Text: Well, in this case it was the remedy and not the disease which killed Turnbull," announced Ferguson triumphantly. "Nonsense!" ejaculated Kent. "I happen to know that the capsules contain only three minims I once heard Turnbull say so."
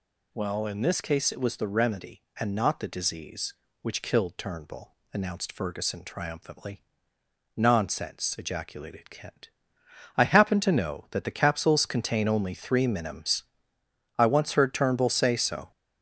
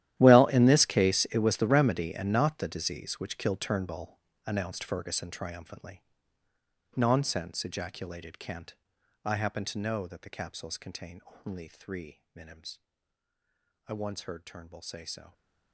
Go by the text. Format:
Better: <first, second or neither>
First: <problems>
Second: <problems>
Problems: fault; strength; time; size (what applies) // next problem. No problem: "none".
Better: first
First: pauses between "minims" and "I"; noticeable; at 13.4 s; 0.74 s long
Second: gets quieter; strong; throughout; 17 dB // pauses between "contain" and "only"; slight; at 11.1 s; 0.28 s long // pauses between "minims" and "I"; at 12.7 s; 1.0 s long